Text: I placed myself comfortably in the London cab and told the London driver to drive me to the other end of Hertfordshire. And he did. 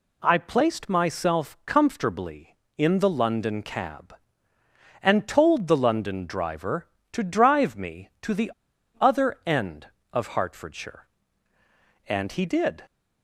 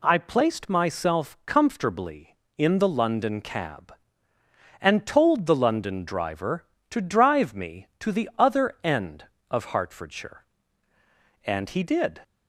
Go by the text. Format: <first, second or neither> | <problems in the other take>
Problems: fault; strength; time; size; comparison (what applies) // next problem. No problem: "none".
second | pauses between "the" and "other"; noticeable; at 8.5 s; 0.50 s long